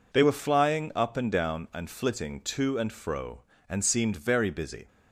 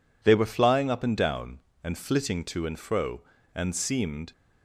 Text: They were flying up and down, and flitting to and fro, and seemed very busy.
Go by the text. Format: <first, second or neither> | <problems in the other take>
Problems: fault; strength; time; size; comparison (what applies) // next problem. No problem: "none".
first | stops before "very busy"; at 4.3 s